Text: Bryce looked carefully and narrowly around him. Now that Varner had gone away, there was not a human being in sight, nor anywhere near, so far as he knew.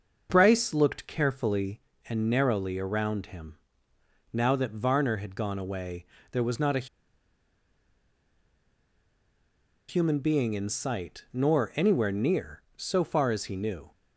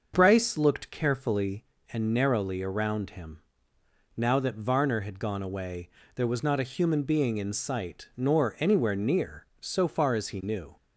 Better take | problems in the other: second | starts louder than the rest; until 1.3 s; 6 dB; also in the second // pauses between "a" and "human"; strong; at 6.8 s; 3.0 s long

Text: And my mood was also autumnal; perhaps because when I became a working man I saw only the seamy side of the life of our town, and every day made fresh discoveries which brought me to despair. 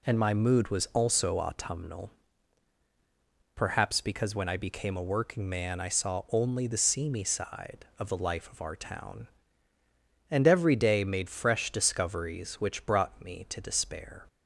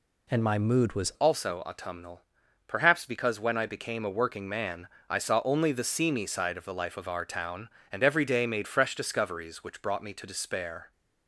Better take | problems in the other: first | changes voice at "also"; from 1.1 s on; 9.8 s long // pauses between "man" and "I"; slight; at 4.8 s; 0.20 s long

